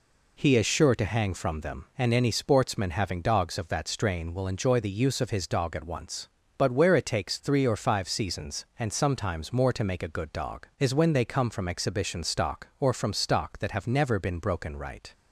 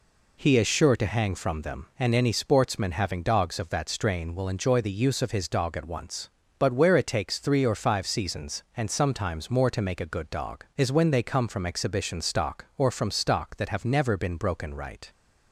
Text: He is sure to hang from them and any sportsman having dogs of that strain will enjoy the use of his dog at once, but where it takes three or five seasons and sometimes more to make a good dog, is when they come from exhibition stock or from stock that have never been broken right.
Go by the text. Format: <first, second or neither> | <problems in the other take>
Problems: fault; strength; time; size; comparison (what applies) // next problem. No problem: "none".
neither | none